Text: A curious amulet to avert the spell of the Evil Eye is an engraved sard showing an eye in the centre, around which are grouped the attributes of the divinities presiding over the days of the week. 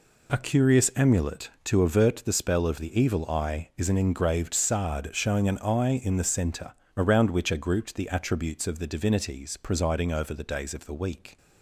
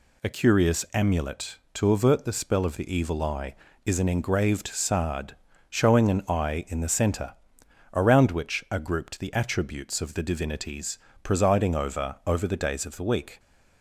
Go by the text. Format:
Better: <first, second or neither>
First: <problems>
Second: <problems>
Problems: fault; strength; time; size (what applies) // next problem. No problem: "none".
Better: first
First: none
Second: pauses between "sard" and "showing"; slight; at 5.3 s; 0.32 s long // pauses between "divinities" and "presiding"; slight; at 10.9 s; 0.26 s long // says "over" twice; at 12.2 s